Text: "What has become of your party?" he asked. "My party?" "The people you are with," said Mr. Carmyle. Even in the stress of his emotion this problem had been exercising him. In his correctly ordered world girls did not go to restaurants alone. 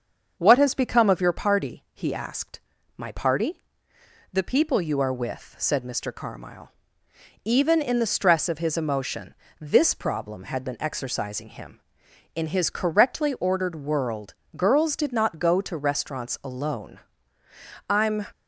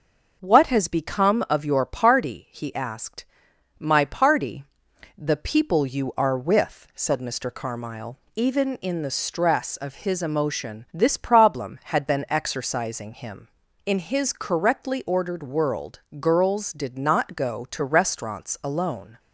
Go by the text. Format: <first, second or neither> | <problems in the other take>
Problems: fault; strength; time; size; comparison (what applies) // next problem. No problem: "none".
second | starts louder than the rest; until 1.4 s; 6.5 dB; also in the second // pauses between "emotion" and "this"; slight; at 9.3 s; 0.26 s long // pauses between "world" and "girls"; slight; at 14.3 s; 0.20 s long; slight in the second // goes on to say "I'm"; slight; from 17.8 s on; 0.38 s long